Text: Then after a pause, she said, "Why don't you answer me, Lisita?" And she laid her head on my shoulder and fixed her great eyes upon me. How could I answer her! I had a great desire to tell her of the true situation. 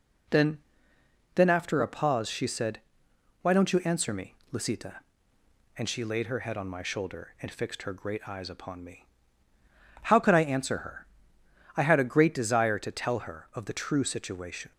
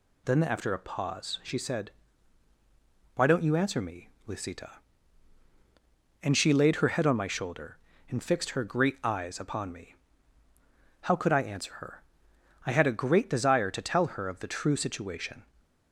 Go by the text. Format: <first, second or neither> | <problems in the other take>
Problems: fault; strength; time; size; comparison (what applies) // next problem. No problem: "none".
second | says "Then" twice; at 1.3 s